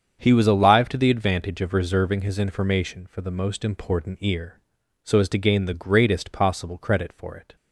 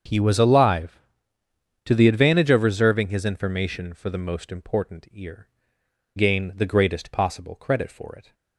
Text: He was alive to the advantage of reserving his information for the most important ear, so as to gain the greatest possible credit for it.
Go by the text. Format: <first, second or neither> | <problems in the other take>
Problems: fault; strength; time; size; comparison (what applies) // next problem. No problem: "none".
first | starts louder than the rest; until 1.9 s; 7 dB; strong in the first // skips "so as to"; at 5.8 s